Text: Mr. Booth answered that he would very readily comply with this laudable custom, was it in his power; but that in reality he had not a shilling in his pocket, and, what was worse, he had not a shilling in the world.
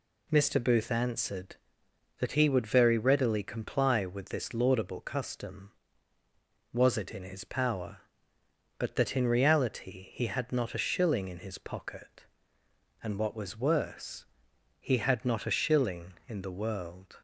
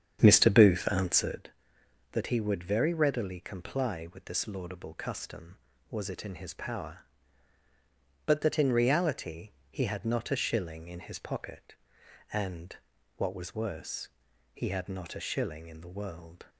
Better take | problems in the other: first | starts louder than the rest; strong; until 1.5 s; 8 dB // pauses between "reality" and "he"; slight; at 9.5 s; 0.18 s long

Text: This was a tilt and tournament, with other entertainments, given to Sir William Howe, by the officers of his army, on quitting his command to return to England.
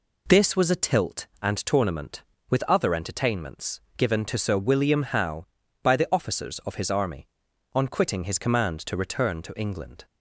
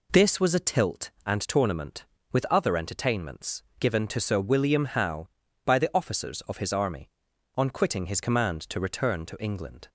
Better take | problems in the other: neither | none

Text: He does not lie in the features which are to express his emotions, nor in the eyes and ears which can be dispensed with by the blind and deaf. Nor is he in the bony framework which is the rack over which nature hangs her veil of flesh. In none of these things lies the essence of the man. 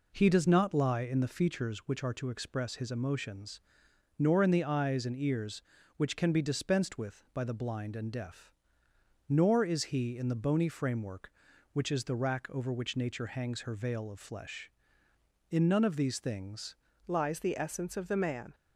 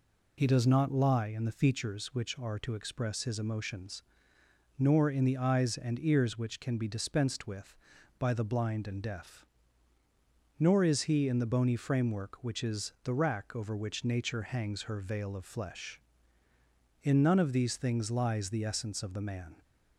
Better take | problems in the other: second | changes voice at "lies"; from 17.0 s on; 1.5 s long

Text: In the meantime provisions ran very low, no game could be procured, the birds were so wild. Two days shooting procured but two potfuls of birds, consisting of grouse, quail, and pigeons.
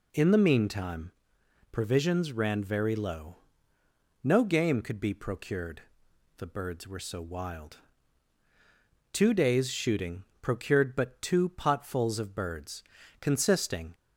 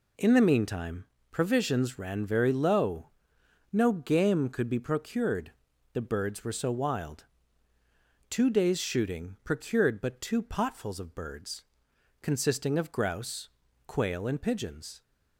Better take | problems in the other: second | pauses between "meantime" and "provisions"; noticeable; at 1.1 s; 0.58 s long; slight in the second // pauses between "shooting" and "procured"; slight; at 10.2 s; 0.18 s long // stops before "of grouse quail and pigeons"; at 13.9 s

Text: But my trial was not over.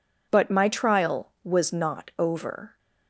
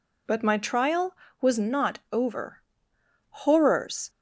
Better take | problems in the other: first | goes on to say "Horrors"; noticeable; from 3.2 s on; 0.80 s long

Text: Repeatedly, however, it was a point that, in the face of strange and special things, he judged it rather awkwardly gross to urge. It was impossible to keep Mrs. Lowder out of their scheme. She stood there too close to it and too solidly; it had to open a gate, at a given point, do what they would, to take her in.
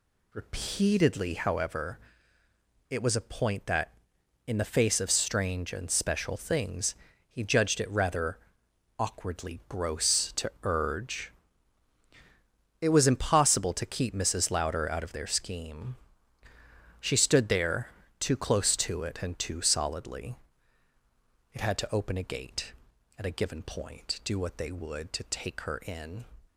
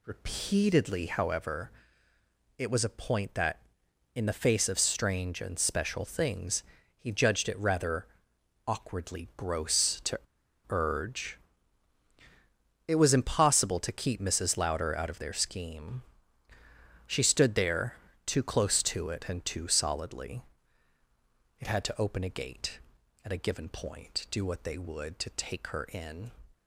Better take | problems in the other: first | pauses between "rather" and "awkwardly"; noticeable; at 8.0 s; 0.60 s long; noticeable in the first // pauses between "to" and "urge"; noticeable; at 10.1 s; 0.50 s long // pauses between "there" and "too"; slight; at 17.9 s; 0.30 s long; slight in the first

